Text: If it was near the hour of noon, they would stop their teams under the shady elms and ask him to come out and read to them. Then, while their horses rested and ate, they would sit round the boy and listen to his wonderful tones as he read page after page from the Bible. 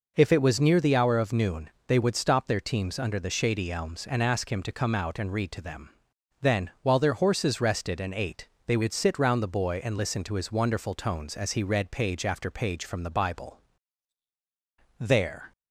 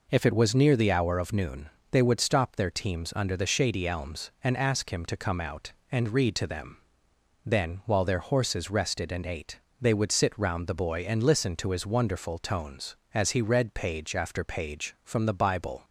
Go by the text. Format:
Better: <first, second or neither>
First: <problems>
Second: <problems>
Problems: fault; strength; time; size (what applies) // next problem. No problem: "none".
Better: second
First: goes on to say "There"; from 14.9 s on; 0.52 s long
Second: none